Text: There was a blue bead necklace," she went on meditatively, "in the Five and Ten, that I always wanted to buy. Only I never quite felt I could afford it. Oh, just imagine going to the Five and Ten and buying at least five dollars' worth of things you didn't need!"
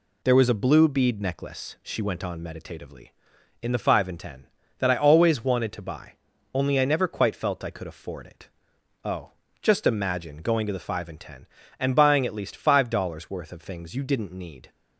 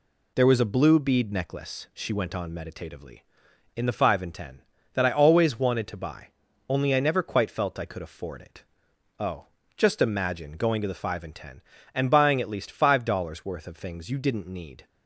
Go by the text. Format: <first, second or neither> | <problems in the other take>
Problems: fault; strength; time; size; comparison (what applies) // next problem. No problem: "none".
neither | none